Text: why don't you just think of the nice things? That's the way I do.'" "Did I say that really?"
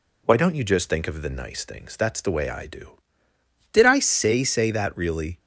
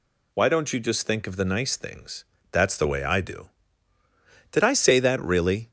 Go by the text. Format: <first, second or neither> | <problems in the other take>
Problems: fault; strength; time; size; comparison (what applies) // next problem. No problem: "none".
second | says "say" twice; at 4.4 s